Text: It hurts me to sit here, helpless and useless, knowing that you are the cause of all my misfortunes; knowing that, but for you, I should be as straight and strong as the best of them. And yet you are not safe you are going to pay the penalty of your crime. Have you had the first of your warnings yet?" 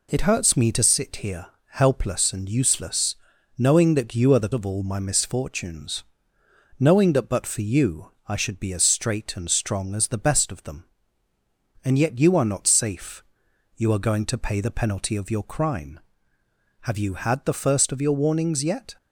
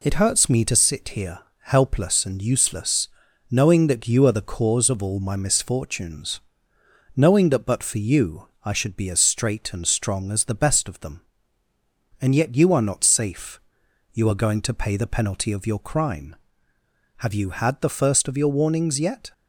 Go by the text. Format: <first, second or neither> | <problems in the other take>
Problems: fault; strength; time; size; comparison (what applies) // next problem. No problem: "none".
second | skips "cause"; at 4.5 s // pauses between "safe" and "you"; noticeable; at 13.2 s; 0.54 s long; noticeable in the second